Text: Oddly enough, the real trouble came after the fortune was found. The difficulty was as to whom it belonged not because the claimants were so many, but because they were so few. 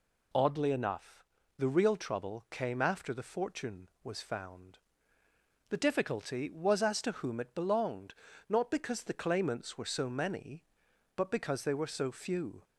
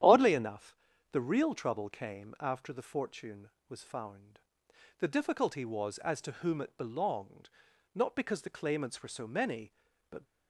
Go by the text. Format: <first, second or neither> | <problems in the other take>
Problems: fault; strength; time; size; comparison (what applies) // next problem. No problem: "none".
first | starts louder than the rest; strong; until 1.4 s; 10.5 dB // pauses between "belonged" and "not"; noticeable; at 7.4 s; 0.46 s long; slight in the first // stops before "because they were so few"; at 10.2 s